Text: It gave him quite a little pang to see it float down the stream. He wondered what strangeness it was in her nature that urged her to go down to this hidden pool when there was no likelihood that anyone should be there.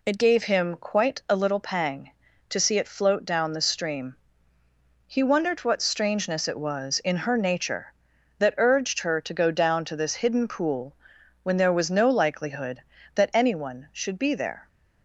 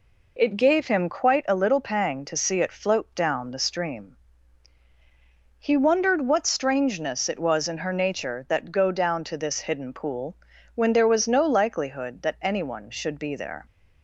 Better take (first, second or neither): first